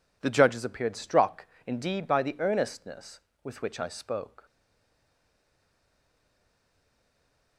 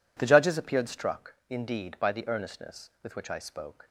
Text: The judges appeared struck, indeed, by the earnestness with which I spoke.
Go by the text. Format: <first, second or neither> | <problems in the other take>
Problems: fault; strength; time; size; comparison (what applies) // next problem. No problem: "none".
second | stays silent after the last word; strong; from 4.4 s on; 3.1 s long